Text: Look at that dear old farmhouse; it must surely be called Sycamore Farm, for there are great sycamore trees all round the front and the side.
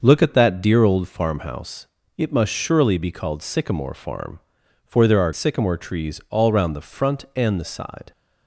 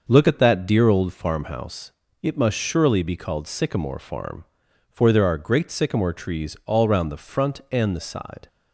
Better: second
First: starts louder than the rest; noticeable; until 1.0 s; 6 dB // skips "great"; at 5.3 s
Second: starts louder than the rest; noticeable; until 1.0 s; 6 dB

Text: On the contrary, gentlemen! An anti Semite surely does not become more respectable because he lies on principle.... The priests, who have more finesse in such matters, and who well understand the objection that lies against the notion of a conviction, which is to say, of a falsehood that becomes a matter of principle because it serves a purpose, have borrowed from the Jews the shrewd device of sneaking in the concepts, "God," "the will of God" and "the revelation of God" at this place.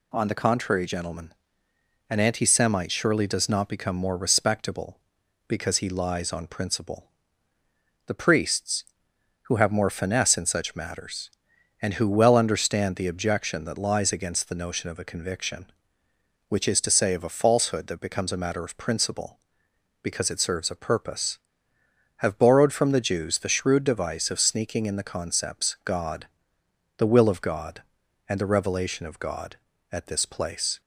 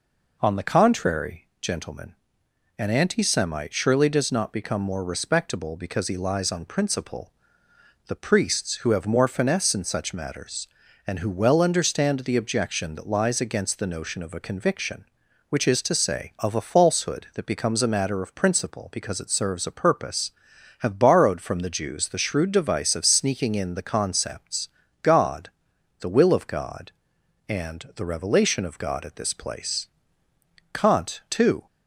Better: first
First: none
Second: goes on to say "Kant too"; noticeable; from 30.7 s on; 0.94 s long

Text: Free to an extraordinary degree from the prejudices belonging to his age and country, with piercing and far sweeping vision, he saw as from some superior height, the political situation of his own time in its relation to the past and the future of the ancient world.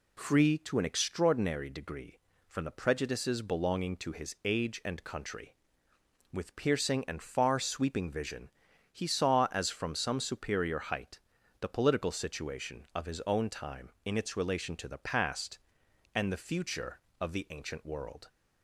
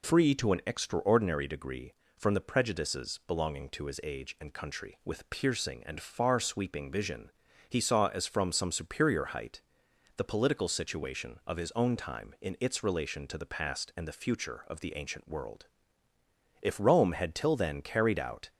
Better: first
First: none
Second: goes on to say "If Rome had till then carried out"; strong; from 16.6 s on; 1.9 s long

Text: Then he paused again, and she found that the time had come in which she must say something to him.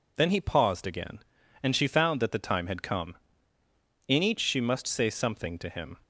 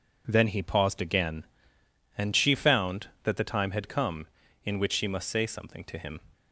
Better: second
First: says "each" for "which"; at 4.2 s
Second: none

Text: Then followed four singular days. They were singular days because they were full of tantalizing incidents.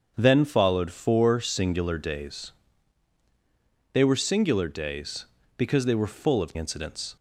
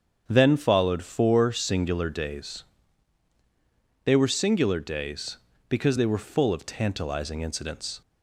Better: second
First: starts louder than the rest; strong; until 1.1 s; 7 dB // skips "tantalizing"; at 6.5 s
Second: starts louder than the rest; strong; until 1.2 s; 7.5 dB

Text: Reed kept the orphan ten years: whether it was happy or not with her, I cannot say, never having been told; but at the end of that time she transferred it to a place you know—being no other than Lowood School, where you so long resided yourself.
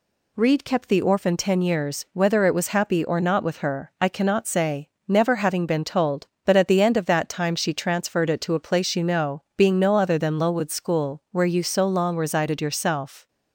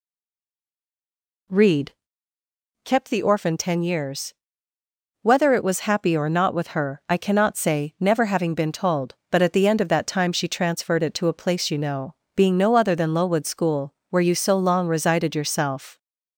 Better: first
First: none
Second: stays silent before the first word; noticeable; until 1.4 s; 1.4 s long // pauses between "Reed" and "kept"; noticeable; at 1.9 s; 0.92 s long

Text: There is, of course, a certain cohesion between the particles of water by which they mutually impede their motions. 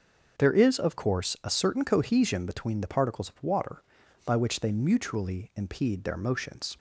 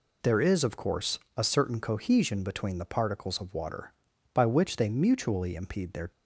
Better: first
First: none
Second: stops before "motions"; at 6.1 s

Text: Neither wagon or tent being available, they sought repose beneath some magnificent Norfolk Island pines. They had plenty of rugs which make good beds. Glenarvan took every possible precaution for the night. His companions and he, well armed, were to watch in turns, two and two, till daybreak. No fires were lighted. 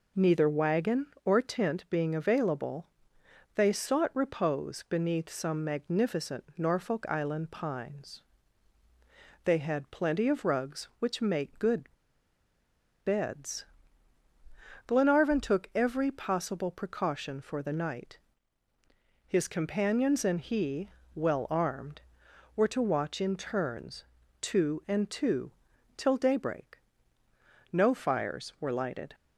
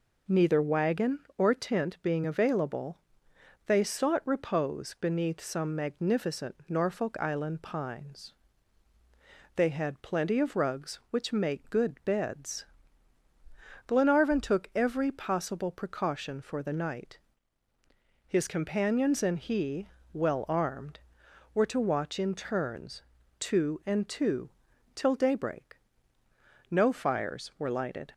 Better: second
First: pauses between "good" and "beds"; at 11.9 s; 1.1 s long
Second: none

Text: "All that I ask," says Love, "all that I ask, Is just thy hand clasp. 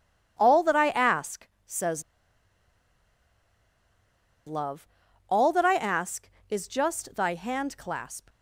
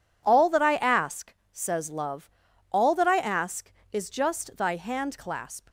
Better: second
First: pauses between "says" and "Love"; strong; at 2.0 s; 2.4 s long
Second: none

